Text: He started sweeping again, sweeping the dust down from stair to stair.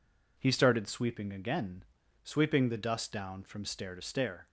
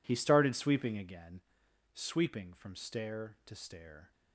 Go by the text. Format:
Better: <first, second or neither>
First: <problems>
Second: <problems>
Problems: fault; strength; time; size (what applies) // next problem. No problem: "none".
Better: first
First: none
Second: skips "the dust down"; at 2.5 s